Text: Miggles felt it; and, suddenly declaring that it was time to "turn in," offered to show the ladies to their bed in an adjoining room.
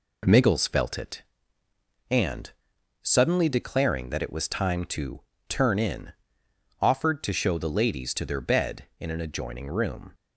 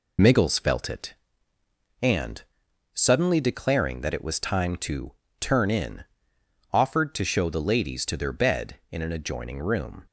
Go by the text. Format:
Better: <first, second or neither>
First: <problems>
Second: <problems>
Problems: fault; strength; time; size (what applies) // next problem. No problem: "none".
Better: first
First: pauses between "to" and "turn"; slight; at 5.1 s; 0.28 s long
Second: loses the start of "Miggles"; at 0.1 s; 45 ms // pauses between "to" and "turn"; slight; at 5.1 s; 0.28 s long